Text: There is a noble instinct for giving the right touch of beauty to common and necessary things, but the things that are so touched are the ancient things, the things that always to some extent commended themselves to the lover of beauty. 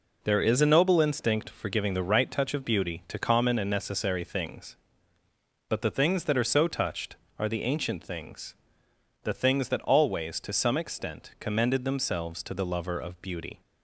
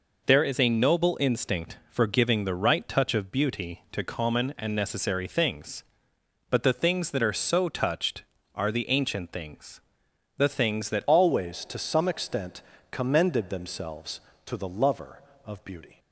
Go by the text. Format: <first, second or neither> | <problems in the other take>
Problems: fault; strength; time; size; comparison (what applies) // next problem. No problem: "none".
first | changes voice at "always"; from 11.0 s on; 4.9 s long // pauses between "extent" and "commended"; slight; at 12.6 s; 0.32 s long